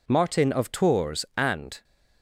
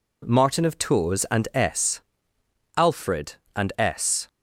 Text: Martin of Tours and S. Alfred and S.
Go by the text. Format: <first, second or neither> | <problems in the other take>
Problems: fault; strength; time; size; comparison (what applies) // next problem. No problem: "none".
second | stops before "S Alfred and S"; at 1.8 s